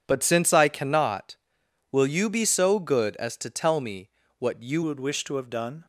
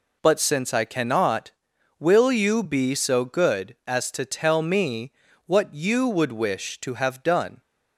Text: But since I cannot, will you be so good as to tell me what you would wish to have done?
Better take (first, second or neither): second